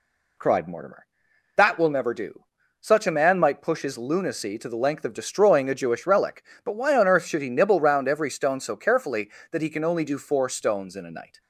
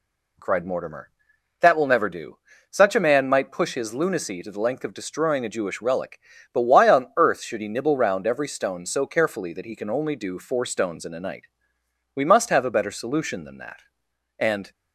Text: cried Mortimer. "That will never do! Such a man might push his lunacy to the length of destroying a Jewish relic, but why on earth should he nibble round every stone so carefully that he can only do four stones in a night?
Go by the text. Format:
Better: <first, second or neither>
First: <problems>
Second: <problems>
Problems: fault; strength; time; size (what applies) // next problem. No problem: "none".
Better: first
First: none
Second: goes on to say "We must have a better solution than that and"; strong; from 12.1 s on; 2.5 s long